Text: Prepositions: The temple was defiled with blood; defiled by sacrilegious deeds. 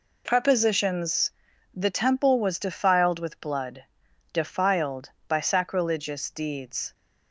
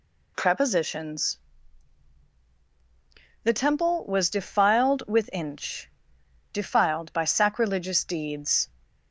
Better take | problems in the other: first | says "inch" for "blood"; at 5.3 s

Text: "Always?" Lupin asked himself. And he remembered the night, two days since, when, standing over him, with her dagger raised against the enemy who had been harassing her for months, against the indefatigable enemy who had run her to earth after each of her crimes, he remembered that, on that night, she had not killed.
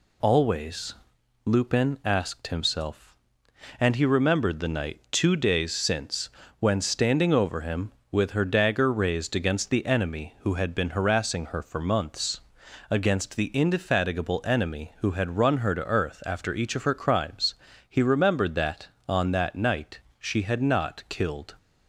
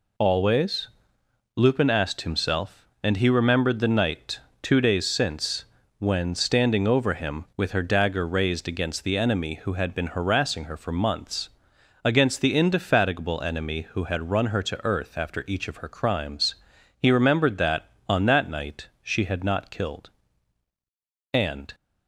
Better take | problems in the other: first | goes on to say "And"; slight; from 21.3 s on; 0.42 s long

